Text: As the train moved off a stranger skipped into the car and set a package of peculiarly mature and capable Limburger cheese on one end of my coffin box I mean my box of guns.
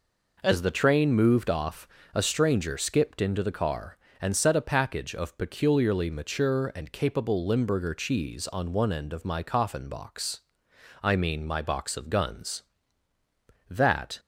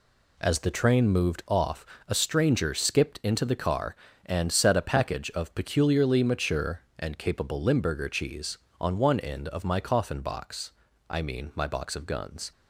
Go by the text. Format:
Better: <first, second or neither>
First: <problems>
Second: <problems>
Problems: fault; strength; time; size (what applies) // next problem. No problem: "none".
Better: second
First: pauses between "off" and "a"; slight; at 1.8 s; 0.26 s long // pauses between "box" and "I"; noticeable; at 10.4 s; 0.60 s long // goes on to say "That"; from 13.6 s on; 0.52 s long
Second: pauses between "off" and "a"; slight; at 1.8 s; 0.22 s long // pauses between "box" and "I"; at 10.7 s; 0.38 s long